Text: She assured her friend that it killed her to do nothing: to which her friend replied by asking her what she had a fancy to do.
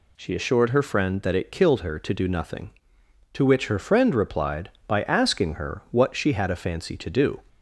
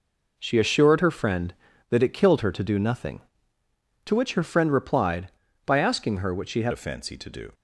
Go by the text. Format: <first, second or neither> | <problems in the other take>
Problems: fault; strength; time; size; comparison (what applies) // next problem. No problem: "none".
first | changes voice at "a"; from 6.7 s on; 0.8 s long